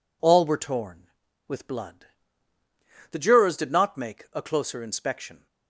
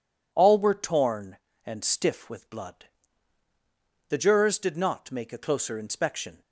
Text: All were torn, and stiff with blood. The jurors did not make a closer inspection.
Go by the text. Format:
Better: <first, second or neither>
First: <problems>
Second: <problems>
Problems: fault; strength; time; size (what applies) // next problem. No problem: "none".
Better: second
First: skips "and stiff"; at 1.2 s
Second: none